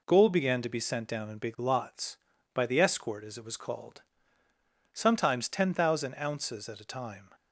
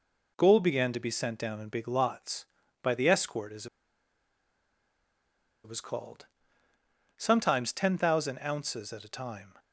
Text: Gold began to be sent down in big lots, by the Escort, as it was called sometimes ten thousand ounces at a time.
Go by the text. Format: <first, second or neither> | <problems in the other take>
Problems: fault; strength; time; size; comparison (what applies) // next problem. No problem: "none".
first | pauses between "as" and "it"; strong; at 3.6 s; 1.9 s long // pauses between "called" and "sometimes"; noticeable; at 6.2 s; 0.94 s long; noticeable in the first